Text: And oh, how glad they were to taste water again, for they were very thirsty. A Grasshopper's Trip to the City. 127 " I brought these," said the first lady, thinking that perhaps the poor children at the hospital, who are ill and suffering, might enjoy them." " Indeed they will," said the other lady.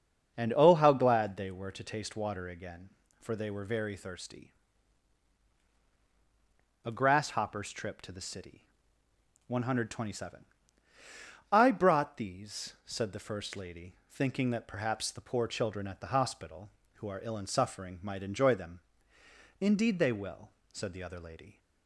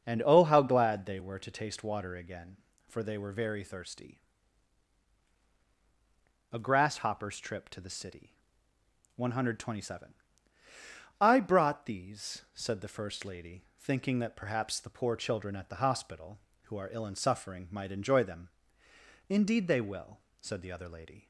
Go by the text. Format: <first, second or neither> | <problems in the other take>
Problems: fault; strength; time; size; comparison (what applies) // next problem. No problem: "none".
neither | starts louder than the rest; the same in both